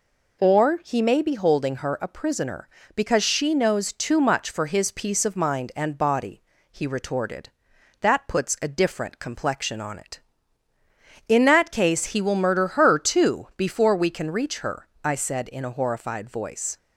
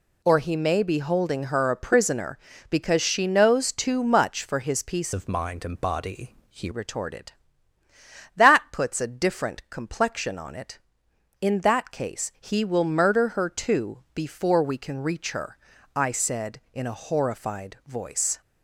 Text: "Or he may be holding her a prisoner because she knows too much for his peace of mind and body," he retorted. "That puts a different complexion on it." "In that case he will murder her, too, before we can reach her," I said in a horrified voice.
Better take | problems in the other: first | changes voice from "of" to "he"; from 5.1 to 6.7 s; 1.6 s long

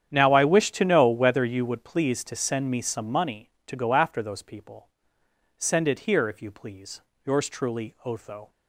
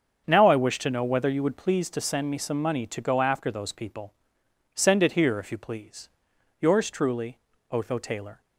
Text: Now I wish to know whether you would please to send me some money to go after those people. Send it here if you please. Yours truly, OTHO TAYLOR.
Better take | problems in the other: second | starts louder than the rest; strong; until 1.1 s; 9 dB; also in the second // stops before "TAYLOR"; at 8.5 s

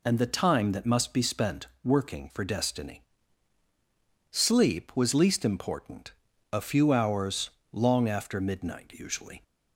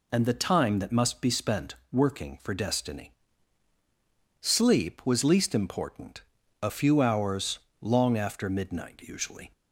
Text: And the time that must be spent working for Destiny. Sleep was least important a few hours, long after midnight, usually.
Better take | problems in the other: neither | pauses between "spent" and "working"; slight; the same in both // pauses between "important" and "a"; the same in both

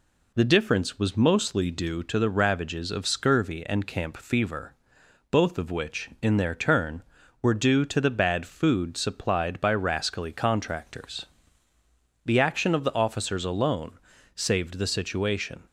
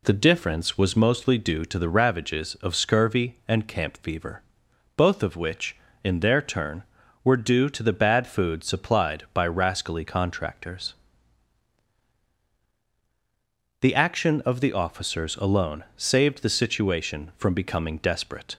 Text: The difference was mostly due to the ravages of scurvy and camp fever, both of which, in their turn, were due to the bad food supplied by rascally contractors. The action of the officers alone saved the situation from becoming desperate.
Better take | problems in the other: second | pauses between "alone" and "saved"; slight; at 13.9 s; 0.36 s long // stops before "from becoming desperate"; at 15.6 s

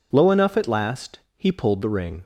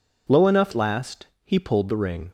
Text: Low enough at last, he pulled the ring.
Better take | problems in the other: first | skips "at"; at 0.7 s

